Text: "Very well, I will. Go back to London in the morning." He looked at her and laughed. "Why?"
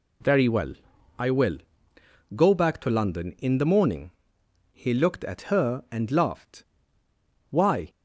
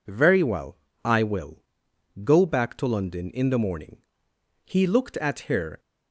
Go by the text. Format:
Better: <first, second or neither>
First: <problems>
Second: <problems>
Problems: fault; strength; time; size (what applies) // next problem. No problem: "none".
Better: first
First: none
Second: stops before "and laughed Why"; at 5.7 s